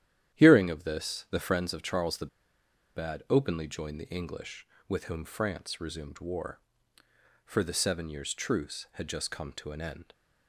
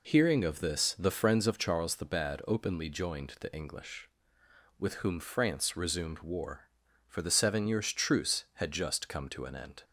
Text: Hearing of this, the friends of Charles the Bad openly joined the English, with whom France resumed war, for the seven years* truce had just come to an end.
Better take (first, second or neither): second